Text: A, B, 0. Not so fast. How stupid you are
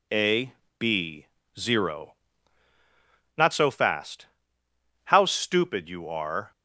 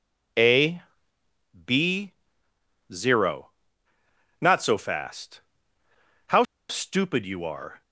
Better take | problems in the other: first | pauses between "How" and "stupid"; slight; at 6.4 s; 0.25 s long

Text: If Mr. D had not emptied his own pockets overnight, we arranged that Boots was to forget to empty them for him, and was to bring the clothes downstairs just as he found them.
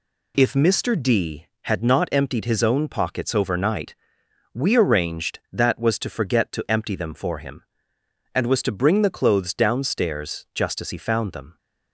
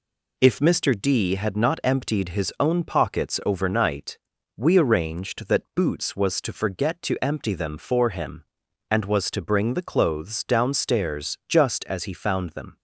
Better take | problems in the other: second | skips "Boots"; at 5.7 s

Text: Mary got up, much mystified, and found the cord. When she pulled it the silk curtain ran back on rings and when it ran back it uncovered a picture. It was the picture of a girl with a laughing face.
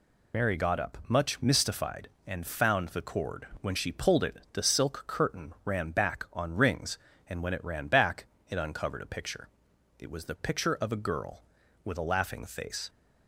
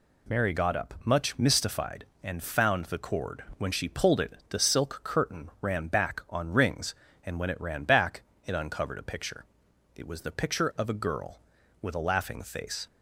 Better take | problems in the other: second | loses the start of "Mary"; at 0.3 s; 50 ms // pauses between "it" and "the"; slight; at 4.3 s; 0.16 s long; slight in the second // pauses between "back" and "it"; slight; at 8.2 s; 0.22 s long; slight in the second

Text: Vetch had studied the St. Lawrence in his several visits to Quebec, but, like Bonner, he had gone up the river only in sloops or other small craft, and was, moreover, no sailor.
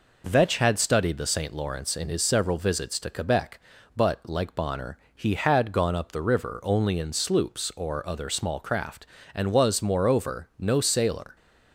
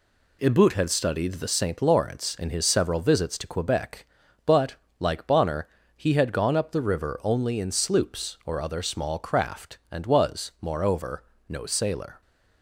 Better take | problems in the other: first | says "Ibut" for "Vetch"; at 0.4 s

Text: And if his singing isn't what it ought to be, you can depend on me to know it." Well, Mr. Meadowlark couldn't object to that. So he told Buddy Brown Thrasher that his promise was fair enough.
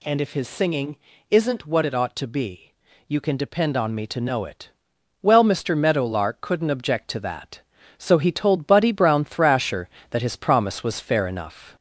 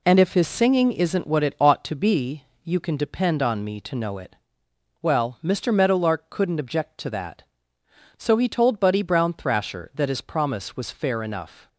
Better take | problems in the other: second | gets louder; slight; throughout; 2 dB // pauses between "singing" and "isn't"; slight; at 0.9 s; 0.34 s long

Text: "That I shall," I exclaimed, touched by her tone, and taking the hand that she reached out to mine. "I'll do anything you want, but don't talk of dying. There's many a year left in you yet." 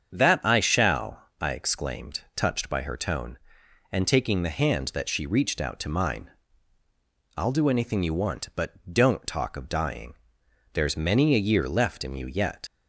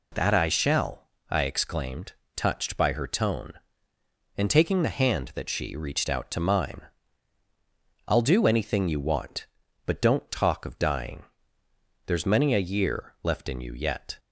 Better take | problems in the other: second | starts louder than the rest; strong; until 1.1 s; 7.5 dB // leaves "yet" unfinished; at 12.6 s; 95 ms

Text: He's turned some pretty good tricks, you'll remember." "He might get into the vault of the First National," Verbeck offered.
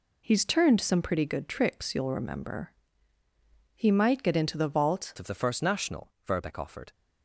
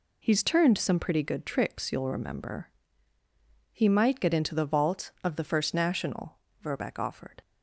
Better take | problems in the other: second | changes voice at "of"; from 5.1 s on; 1.8 s long

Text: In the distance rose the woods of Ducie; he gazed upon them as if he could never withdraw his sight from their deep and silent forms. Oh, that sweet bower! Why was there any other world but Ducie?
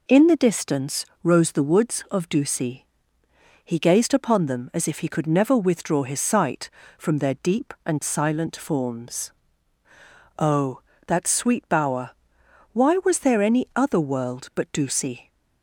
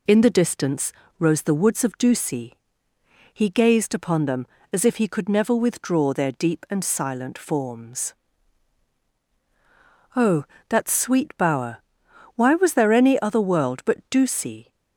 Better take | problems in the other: first | pauses between "distance" and "rose"; slight; at 0.9 s; 0.26 s long; slight in the first // skips "his sight from"; at 6.1 s

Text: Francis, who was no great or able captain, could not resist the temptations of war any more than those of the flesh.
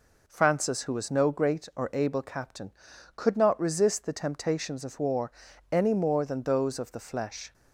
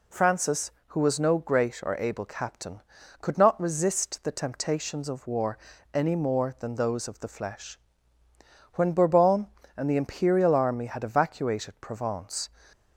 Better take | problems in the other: first | pauses between "war" and "any"; at 5.5 s; 0.38 s long; also in the first // goes on to say "When Bourbon and the imperial army had evacuated Provence"; strong; from 8.7 s on; 3.7 s long

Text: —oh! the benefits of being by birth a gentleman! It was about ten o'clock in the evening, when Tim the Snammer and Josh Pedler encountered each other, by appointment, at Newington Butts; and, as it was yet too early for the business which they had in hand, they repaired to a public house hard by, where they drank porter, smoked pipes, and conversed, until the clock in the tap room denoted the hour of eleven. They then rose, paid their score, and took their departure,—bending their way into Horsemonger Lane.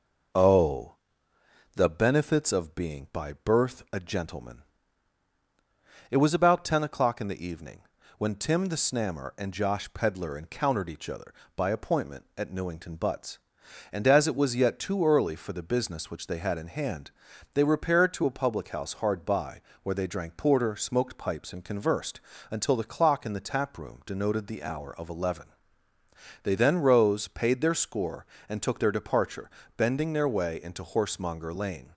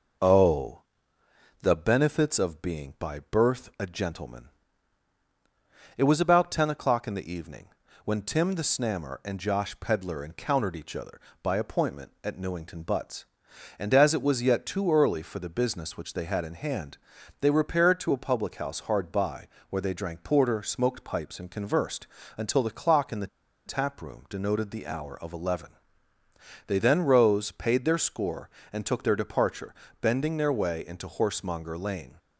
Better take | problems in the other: first | pauses between "the" and "tap"; at 23.2 s; 0.39 s long

